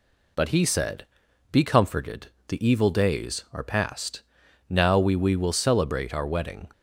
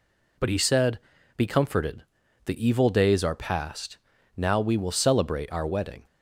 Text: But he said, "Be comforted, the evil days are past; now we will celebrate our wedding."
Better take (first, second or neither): second